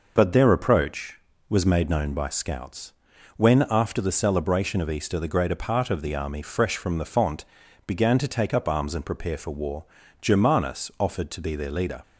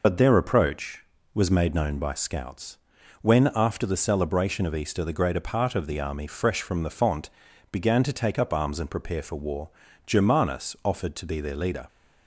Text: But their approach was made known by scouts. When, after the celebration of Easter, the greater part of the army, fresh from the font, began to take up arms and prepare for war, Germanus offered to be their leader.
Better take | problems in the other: first | loses the start of "But"; at 0.0 s; 40 ms

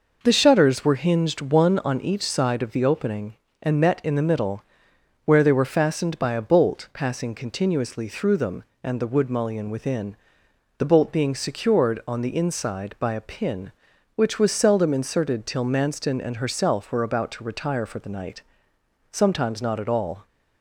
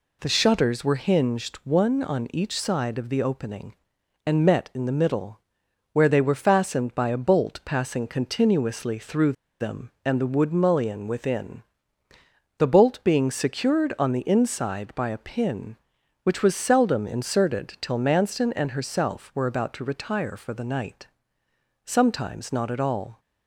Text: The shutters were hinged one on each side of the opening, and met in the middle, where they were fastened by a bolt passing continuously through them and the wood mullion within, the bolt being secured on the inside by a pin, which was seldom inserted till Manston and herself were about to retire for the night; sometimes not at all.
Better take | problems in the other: first | pauses between "through" and "them"; slight; at 9.3 s; 0.28 s long

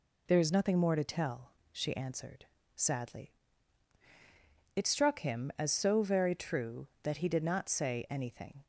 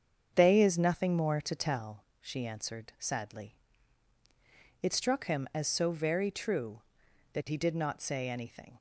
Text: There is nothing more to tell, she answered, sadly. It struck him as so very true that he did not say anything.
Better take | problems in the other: first | starts louder than the rest; strong; until 1.3 s; 7 dB // says "They" for "There"; at 0.3 s

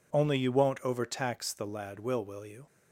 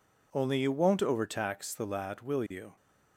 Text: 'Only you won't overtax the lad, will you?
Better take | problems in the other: second | says "will" twice; at 2.2 s

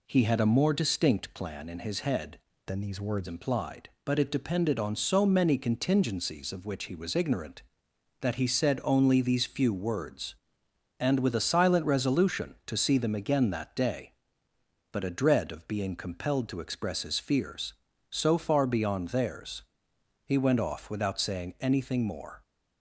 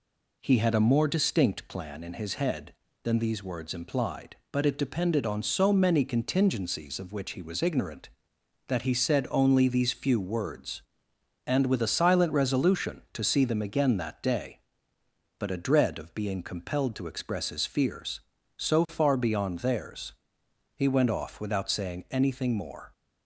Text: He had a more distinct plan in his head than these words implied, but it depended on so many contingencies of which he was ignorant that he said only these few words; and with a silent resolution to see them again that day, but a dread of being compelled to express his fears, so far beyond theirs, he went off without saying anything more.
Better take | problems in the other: second | changes voice from "than" to "words"; from 2.6 to 3.2 s; 0.6 s long

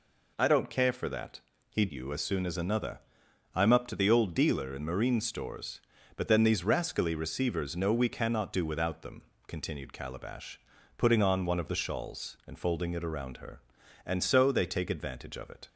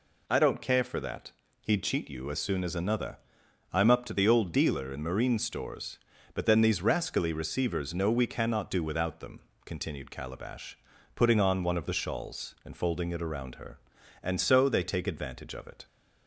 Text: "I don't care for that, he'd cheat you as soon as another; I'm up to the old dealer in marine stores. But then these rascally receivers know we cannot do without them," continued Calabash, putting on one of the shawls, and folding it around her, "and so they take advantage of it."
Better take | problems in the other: second | skips "cheat"; at 1.9 s

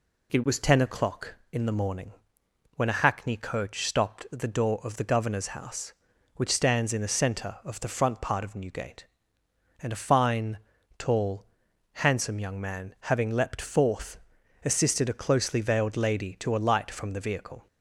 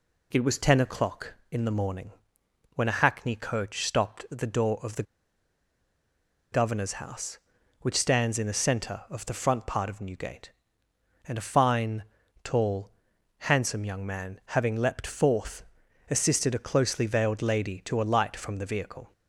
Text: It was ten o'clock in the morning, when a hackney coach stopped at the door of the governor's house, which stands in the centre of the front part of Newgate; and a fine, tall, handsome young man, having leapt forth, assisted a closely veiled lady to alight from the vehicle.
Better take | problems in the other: first | pauses between "the" and "governor's"; strong; at 5.0 s; 1.4 s long

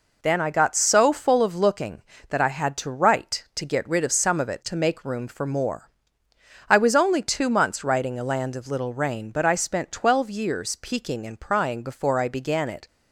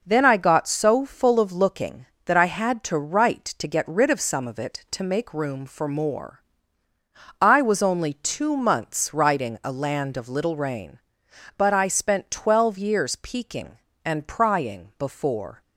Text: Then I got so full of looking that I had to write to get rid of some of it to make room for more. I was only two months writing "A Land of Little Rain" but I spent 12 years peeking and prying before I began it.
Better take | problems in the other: first | stops before "I began it"; at 15.6 s

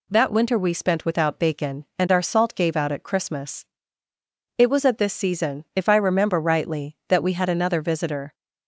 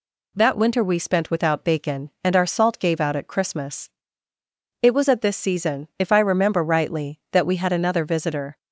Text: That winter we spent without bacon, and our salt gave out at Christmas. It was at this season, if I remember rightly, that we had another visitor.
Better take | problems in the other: neither | none

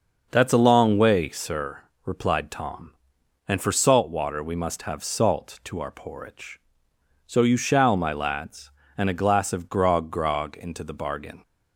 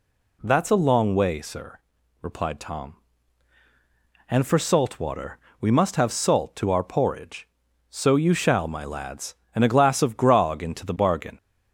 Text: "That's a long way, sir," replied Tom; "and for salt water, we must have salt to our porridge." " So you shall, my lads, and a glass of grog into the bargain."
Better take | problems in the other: second | starts louder than the rest; until 1.3 s; 6.5 dB // says "grog" twice; at 10.1 s

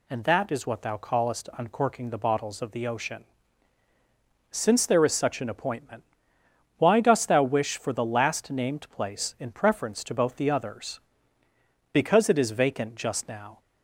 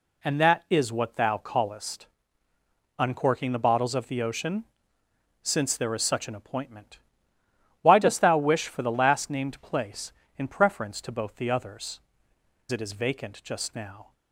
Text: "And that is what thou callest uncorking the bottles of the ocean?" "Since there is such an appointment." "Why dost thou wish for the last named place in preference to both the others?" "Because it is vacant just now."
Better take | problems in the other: first | pauses between "callest" and "uncorking"; noticeable; at 2.0 s; 0.92 s long // skips "Because"; at 12.3 s

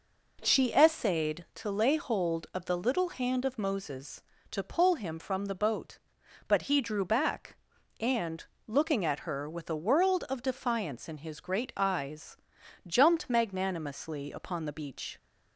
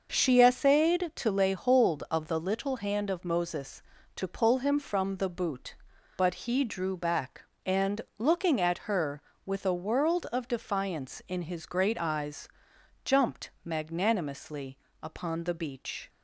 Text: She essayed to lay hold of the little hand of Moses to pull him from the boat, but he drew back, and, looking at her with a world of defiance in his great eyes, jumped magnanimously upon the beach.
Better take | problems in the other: first | says "boot" for "boat"; at 5.2 s // pauses between "magnanimously" and "upon"; slight; at 14.7 s; 0.24 s long

